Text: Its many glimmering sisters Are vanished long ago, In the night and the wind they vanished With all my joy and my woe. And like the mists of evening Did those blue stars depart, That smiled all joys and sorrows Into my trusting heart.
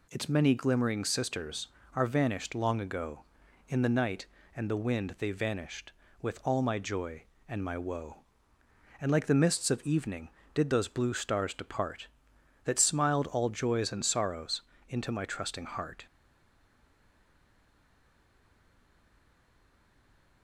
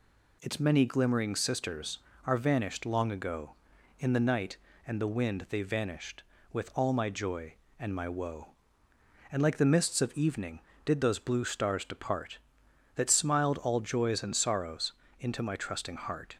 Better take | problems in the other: second | pauses between "sorrows" and "Into"; slight; at 14.6 s; 0.26 s long; slight in the second // stays silent after the last word; strong; from 16.0 s on; 4.4 s long

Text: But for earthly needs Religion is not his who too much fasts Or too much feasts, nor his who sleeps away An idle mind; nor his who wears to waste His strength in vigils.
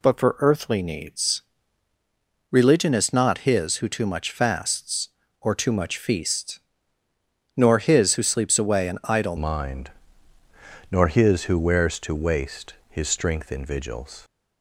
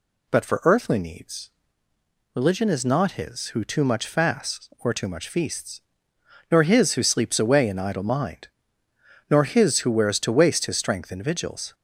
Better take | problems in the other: second | pauses between "needs" and "Religion"; at 1.4 s; 1.0 s long; noticeable in the second // changes voice at "mind"; from 9.3 s on; 4.9 s long // pauses between "waste" and "His"; slight; at 12.7 s; 0.18 s long

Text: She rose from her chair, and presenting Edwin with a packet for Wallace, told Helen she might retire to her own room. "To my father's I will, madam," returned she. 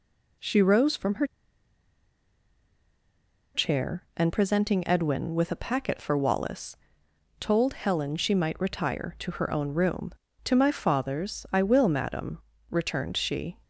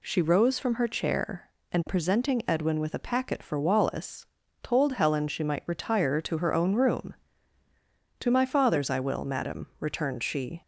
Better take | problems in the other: second | pauses between "her" and "chair"; strong; at 1.2 s; 2.2 s long

